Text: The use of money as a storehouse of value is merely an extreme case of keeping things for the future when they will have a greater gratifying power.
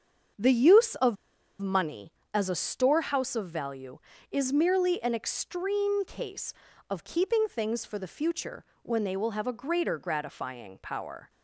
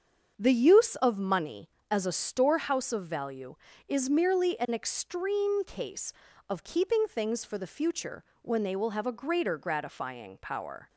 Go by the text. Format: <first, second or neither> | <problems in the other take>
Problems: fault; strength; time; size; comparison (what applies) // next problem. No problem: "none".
second | starts louder than the rest; strong; until 1.8 s; 7 dB; strong in the second // pauses between "of" and "money"; at 1.1 s; 0.43 s long // pauses between "future" and "when"; slight; at 8.6 s; 0.20 s long; slight in the second